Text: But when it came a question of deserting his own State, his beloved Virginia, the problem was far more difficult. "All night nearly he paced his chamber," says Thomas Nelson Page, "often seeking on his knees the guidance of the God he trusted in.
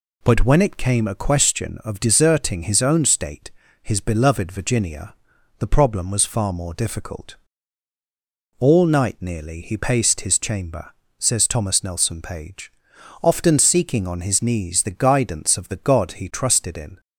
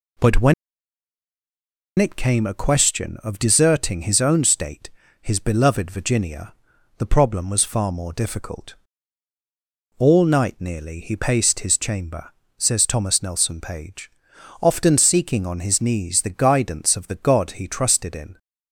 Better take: first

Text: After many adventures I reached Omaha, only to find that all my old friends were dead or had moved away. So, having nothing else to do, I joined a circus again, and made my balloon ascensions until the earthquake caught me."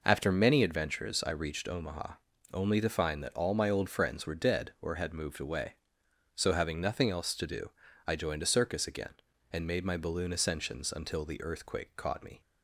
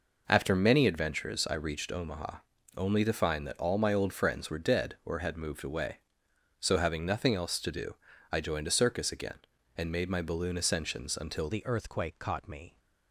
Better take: first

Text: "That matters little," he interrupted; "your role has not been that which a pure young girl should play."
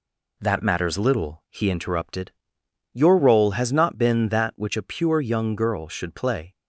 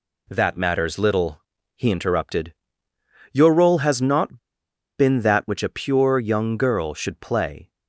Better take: first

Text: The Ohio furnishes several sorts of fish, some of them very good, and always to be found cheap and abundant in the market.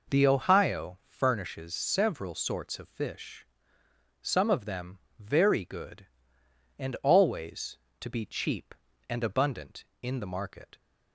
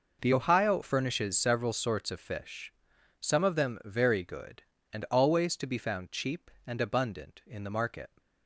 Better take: second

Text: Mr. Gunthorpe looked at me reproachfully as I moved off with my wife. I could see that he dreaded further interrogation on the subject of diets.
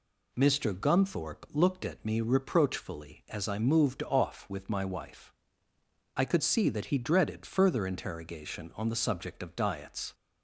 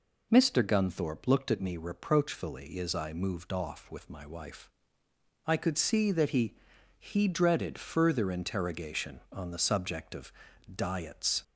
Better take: first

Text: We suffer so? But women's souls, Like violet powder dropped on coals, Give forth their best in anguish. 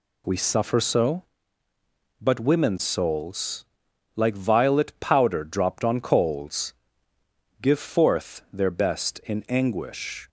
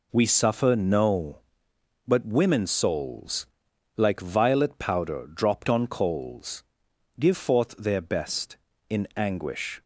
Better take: first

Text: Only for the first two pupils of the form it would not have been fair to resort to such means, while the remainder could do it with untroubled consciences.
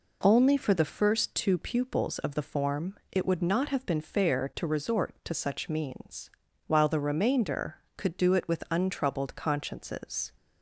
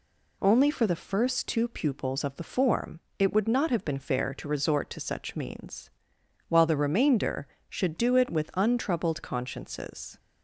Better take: first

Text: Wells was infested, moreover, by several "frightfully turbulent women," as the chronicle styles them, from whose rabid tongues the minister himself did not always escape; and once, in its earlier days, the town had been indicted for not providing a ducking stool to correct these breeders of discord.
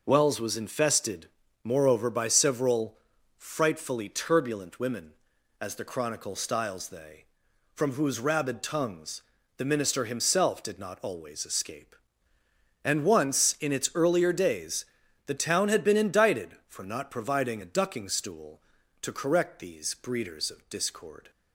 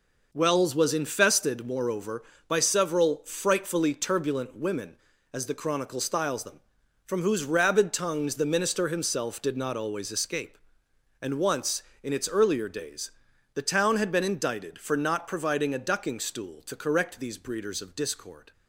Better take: second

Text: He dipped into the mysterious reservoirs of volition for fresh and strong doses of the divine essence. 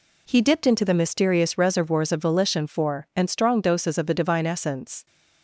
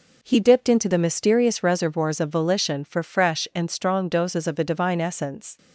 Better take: second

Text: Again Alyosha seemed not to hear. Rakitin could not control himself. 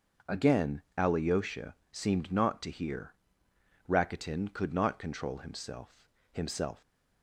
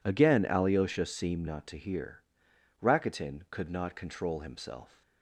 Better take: second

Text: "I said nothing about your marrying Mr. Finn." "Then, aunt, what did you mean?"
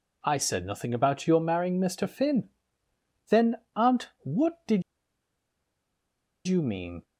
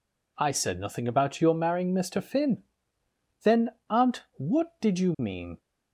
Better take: second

